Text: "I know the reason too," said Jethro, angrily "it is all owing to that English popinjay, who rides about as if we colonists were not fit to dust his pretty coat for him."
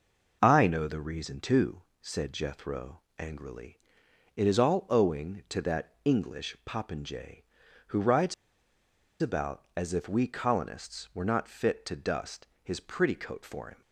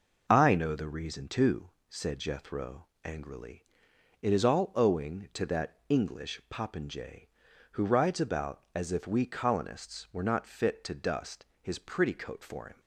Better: second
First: pauses between "angrily" and "it"; noticeable; at 3.7 s; 0.60 s long // pauses between "rides" and "about"; noticeable; at 8.3 s; 0.88 s long // pauses between "dust" and "his"; slight; at 12.4 s; 0.18 s long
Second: pauses between "angrily" and "it"; noticeable; at 3.6 s; 0.60 s long // pauses between "dust" and "his"; slight; at 11.4 s; 0.18 s long

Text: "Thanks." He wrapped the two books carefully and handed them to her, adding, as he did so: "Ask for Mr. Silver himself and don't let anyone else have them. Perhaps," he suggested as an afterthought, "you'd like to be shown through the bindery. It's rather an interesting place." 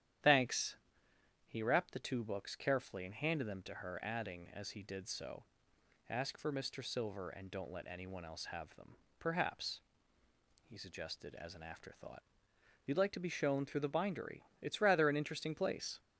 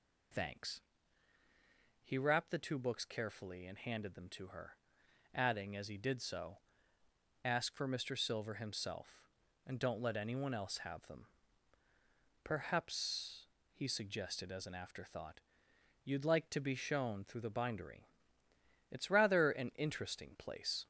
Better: second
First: starts louder than the rest; strong; until 1.9 s; 10.5 dB // skips "himself"; at 7.2 s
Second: none

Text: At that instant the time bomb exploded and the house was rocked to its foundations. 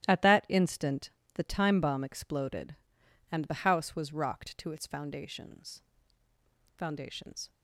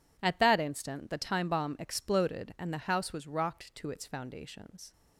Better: second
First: starts louder than the rest; strong; until 1.1 s; 13 dB // pauses between "instant" and "the"; slight; at 1.1 s; 0.24 s long // says "foundations" twice; at 6.7 s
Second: none

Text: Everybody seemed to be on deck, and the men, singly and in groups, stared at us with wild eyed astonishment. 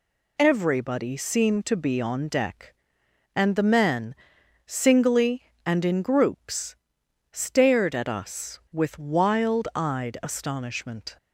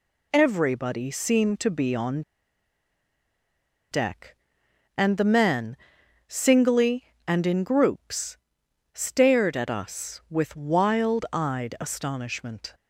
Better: first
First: none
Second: pauses between "on" and "deck"; strong; at 2.2 s; 1.7 s long

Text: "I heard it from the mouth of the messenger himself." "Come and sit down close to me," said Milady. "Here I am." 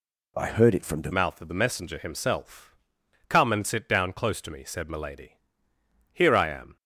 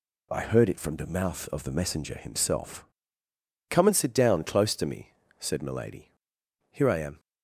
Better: second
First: changes voice at "mouth"; from 1.1 s on; 5.6 s long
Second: none

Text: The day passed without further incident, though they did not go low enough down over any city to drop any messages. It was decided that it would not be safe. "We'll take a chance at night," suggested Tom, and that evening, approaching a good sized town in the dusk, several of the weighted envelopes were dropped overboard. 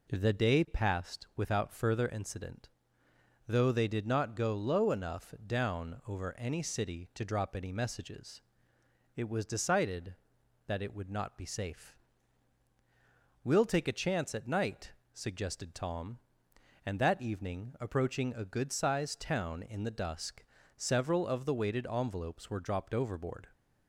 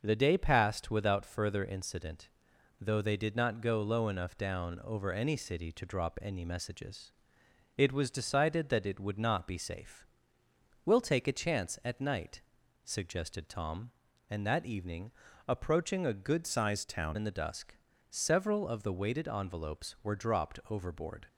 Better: first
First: none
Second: starts louder than the rest; noticeable; until 1.0 s; 6 dB // changes voice from "sized" to "town"; from 16.4 to 17.1 s; 0.7 s long

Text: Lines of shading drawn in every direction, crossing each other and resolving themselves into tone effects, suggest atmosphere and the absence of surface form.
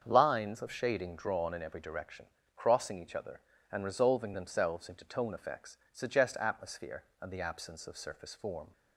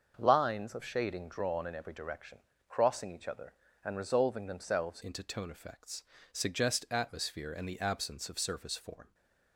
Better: first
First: starts louder than the rest; until 1.0 s; 7 dB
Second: starts louder than the rest; until 1.1 s; 6.5 dB // changes voice at "into"; from 5.0 s on; 4.1 s long // stays silent after the last word; slight; from 9.0 s on; 0.5 s long

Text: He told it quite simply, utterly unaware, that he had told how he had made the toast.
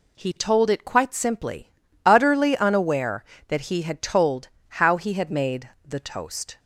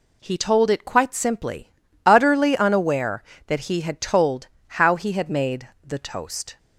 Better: neither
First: pauses between "told" and "how"; slight; at 4.4 s; 0.18 s long // pauses between "made" and "the"; slight; at 5.6 s; 0.18 s long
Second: pauses between "told" and "how"; slight; at 4.4 s; 0.18 s long // pauses between "made" and "the"; slight; at 5.6 s; 0.18 s long

